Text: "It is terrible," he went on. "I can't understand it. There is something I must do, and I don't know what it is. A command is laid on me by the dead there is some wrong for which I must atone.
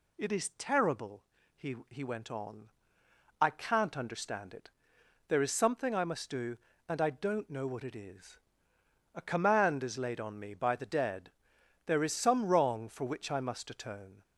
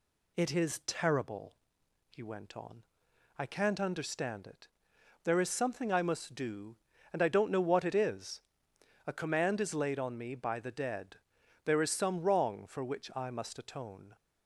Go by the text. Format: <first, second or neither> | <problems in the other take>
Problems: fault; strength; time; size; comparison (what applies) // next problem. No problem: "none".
second | says "he" twice; at 1.8 s // pauses between "dead" and "there"; noticeable; at 11.3 s; 0.54 s long; noticeable in the second